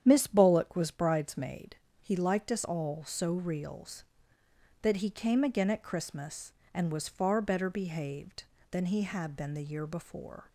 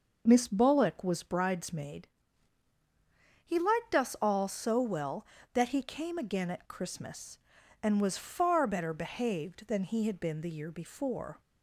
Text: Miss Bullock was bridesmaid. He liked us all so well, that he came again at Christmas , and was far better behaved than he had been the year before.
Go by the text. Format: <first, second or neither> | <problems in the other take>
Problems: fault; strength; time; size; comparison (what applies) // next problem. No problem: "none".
second | starts louder than the rest; strong; until 1.0 s; 9 dB // says "reals" for "well"; at 3.3 s